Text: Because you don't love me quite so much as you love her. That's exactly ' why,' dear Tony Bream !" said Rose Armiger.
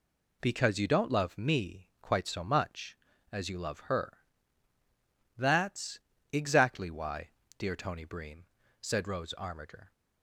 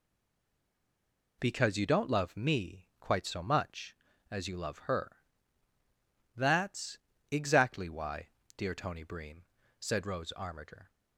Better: first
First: pauses between "That's" and "exactly"; slight; at 5.9 s; 0.32 s long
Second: stays silent before the first word; noticeable; until 1.4 s; 1.4 s long // pauses between "That's" and "exactly"; slight; at 6.9 s; 0.32 s long

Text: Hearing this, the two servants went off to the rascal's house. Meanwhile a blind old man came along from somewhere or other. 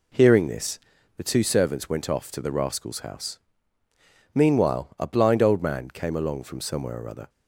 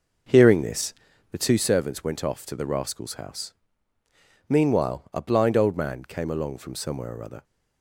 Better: first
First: none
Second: starts louder than the rest; noticeable; until 1.8 s; 6 dB

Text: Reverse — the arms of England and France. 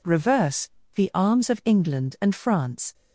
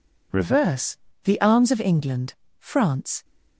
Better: first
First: none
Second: skips "and"; at 2.4 s

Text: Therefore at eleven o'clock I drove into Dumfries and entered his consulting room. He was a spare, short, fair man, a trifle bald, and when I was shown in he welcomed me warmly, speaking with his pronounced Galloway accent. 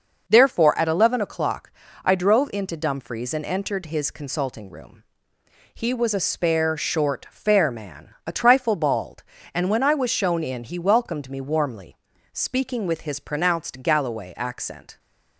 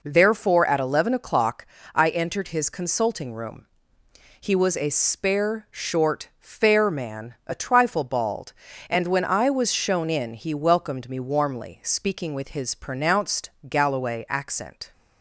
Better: first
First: pauses between "o'clock" and "I"; slight; at 1.7 s; 0.32 s long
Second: pauses between "o'clock" and "I"; slight; at 1.6 s; 0.28 s long // skips "drove into Dumfries and"; at 2.0 s // pauses between "pronounced" and "Galloway"; slight; at 13.4 s; 0.18 s long

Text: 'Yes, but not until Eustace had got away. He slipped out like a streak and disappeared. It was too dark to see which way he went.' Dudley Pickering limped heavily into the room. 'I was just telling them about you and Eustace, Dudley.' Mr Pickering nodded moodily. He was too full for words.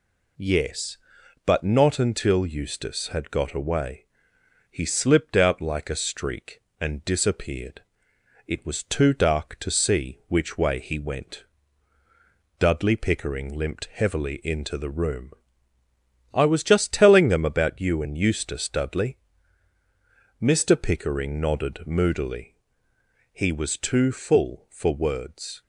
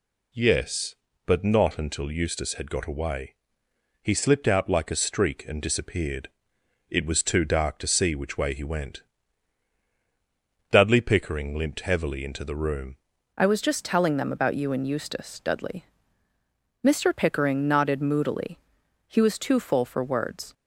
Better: first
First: none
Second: changes voice at "I"; from 13.3 s on; 7.2 s long

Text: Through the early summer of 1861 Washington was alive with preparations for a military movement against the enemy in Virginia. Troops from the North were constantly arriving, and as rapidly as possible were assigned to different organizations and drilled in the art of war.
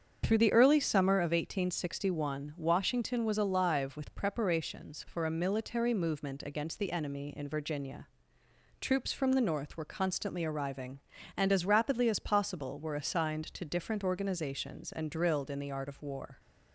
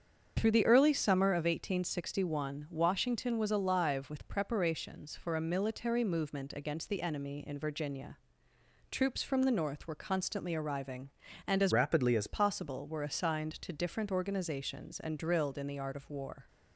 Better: first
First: starts louder than the rest; strong; until 1.2 s; 7.5 dB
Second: starts louder than the rest; strong; until 1.3 s; 7.5 dB // changes voice from "rapidly" to "as"; from 11.7 to 12.2 s; 0.5 s long

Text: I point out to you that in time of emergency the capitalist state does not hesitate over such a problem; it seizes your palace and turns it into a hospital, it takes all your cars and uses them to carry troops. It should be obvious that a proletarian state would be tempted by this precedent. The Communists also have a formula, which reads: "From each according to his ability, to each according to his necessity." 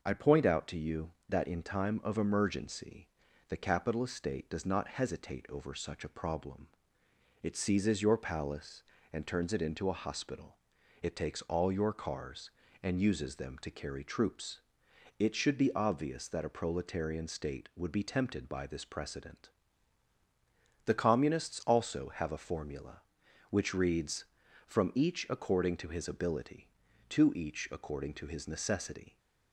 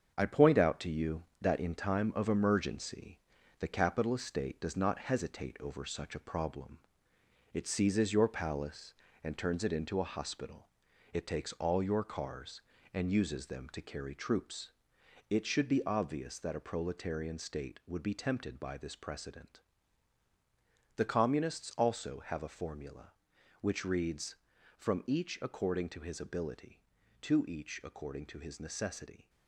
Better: first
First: pauses between "emergency" and "the"; at 3.0 s; 0.42 s long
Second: gets quieter; throughout; 6.5 dB // pauses between "emergency" and "the"; at 3.1 s; 0.42 s long

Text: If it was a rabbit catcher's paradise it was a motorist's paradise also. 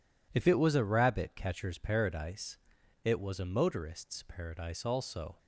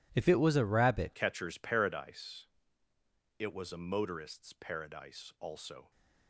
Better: first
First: pauses between "paradise" and "it"; noticeable; at 2.5 s; 0.46 s long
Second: changes voice at "catcher's"; from 1.1 s on; 4.8 s long // pauses between "paradise" and "it"; noticeable; at 2.4 s; 0.92 s long

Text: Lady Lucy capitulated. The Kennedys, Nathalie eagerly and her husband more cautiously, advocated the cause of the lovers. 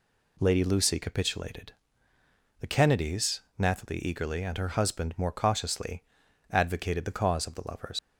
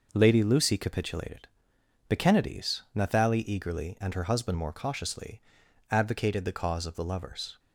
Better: second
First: leaves "lovers" unfinished; at 7.9 s; 95 ms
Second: none

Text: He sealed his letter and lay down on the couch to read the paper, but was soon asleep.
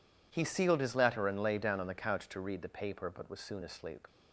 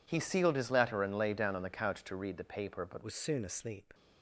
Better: first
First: none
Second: changes voice at "was"; from 3.0 s on; 0.9 s long

